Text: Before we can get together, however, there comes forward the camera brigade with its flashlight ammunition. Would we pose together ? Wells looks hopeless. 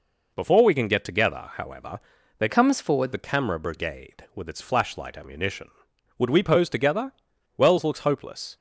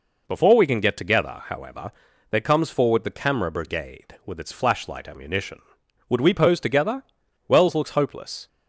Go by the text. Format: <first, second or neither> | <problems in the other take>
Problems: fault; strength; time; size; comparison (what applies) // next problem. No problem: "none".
second | changes voice from "comes" to "forward"; from 2.4 to 3.1 s; 0.7 s long